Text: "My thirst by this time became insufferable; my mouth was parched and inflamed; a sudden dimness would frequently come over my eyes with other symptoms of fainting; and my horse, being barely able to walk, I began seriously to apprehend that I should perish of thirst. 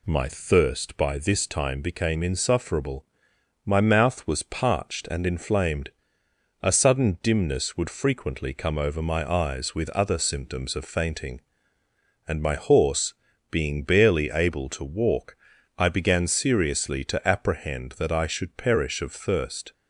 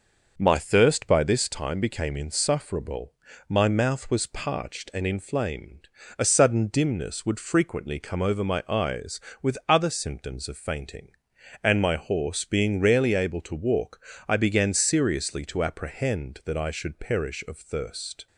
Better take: first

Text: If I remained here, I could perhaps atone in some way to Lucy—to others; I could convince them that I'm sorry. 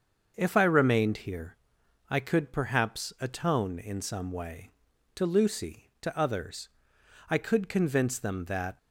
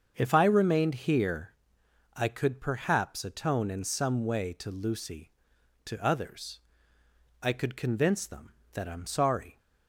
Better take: second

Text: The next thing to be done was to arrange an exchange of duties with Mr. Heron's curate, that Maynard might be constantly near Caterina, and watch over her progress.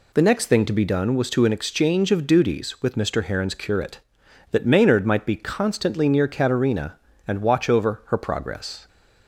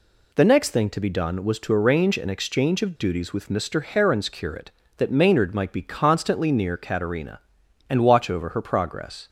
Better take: second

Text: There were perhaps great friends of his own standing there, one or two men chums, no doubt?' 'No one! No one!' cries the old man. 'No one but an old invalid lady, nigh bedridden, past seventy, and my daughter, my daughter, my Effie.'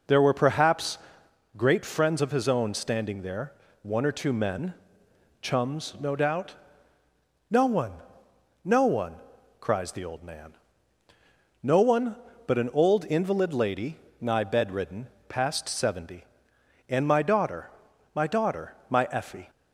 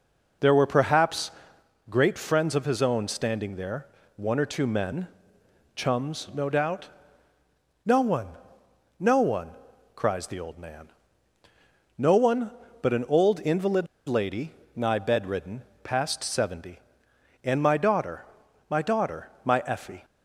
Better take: first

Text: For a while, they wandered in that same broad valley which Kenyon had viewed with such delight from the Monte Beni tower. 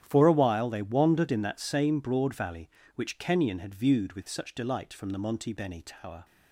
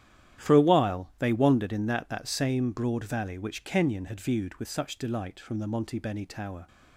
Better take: first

